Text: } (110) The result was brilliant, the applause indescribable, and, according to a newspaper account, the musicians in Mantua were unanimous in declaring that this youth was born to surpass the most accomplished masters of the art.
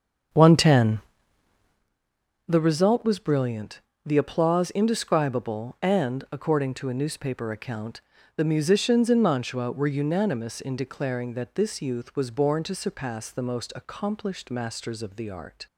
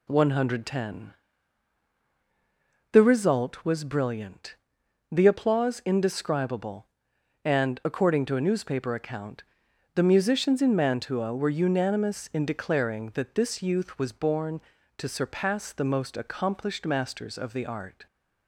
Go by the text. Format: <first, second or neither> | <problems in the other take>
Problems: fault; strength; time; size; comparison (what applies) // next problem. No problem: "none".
second | starts louder than the rest; until 1.8 s; 7 dB